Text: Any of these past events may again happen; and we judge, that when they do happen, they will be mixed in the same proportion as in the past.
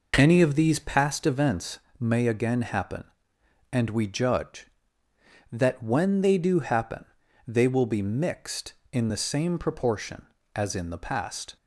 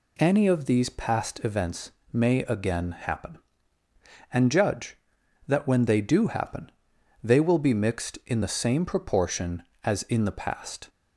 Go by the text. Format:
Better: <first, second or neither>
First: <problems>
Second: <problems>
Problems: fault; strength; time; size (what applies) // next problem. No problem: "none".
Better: first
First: pauses between "events" and "may"; slight; at 1.8 s; 0.18 s long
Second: pauses between "events" and "may"; slight; at 1.9 s; 0.20 s long // skips "we"; at 4.4 s